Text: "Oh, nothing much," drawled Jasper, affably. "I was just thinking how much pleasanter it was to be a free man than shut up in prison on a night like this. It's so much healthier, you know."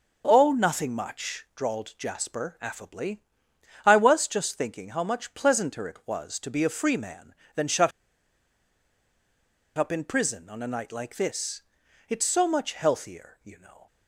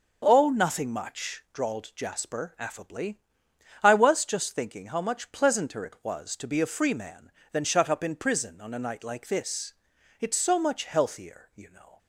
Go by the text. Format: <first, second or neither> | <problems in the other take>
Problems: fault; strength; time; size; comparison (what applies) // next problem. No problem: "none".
second | pauses between "shut" and "up"; strong; at 7.9 s; 1.8 s long